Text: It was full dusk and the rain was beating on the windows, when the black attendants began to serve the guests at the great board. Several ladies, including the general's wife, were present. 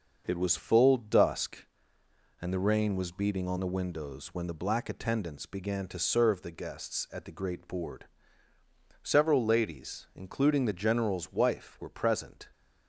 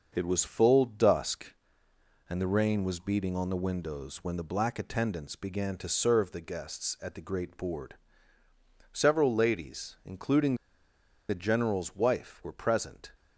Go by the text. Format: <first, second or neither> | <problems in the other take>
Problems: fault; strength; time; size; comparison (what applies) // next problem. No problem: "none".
first | starts louder than the rest; noticeable; until 1.1 s; 6 dB; noticeable in the first // pauses between "including" and "the"; noticeable; at 10.5 s; 0.73 s long